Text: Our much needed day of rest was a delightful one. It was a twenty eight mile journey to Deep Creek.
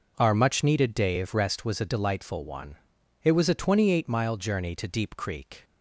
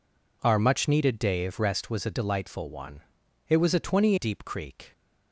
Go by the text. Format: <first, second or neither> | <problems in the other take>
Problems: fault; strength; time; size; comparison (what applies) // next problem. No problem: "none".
first | skips "eight mile journey to"; at 4.1 s